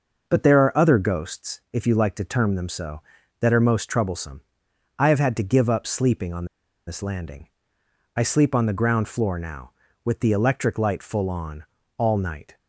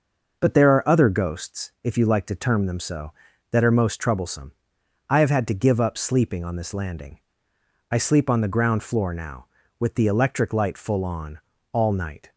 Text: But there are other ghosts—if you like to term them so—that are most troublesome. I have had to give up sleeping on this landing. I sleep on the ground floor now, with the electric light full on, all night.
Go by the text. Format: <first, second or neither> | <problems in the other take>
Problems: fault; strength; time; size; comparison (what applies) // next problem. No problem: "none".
second | pauses between "on" and "this"; at 6.4 s; 0.40 s long